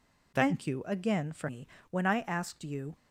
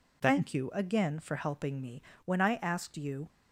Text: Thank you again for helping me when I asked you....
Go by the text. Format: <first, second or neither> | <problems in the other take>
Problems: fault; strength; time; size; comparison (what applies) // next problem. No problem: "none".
second | skips "helping"; at 1.4 s // pauses between "me" and "when"; slight; at 1.6 s; 0.24 s long; slight in the second